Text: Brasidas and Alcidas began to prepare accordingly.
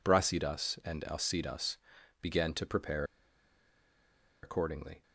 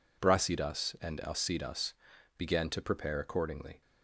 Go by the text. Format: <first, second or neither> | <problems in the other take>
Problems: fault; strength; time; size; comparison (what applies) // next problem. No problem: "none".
second | pauses between "Alcidas" and "began"; at 1.7 s; 0.44 s long; also in the second // pauses between "prepare" and "accordingly"; strong; at 3.0 s; 1.3 s long